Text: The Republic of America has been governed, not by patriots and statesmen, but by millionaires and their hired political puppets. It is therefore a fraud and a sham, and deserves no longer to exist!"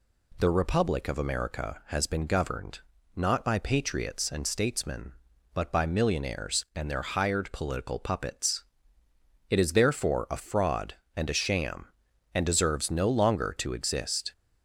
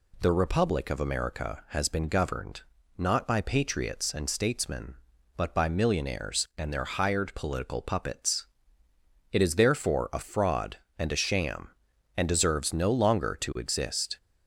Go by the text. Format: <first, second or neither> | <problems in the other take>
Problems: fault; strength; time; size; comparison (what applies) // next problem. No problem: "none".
neither | none